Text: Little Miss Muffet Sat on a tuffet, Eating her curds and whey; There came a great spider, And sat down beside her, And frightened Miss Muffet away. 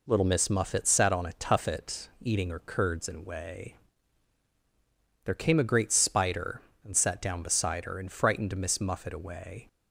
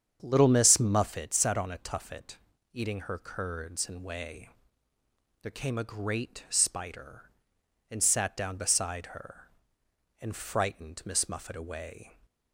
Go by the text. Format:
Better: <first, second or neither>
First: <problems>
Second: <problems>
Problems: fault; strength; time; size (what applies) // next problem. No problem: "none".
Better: first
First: none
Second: starts louder than the rest; strong; until 1.2 s; 8 dB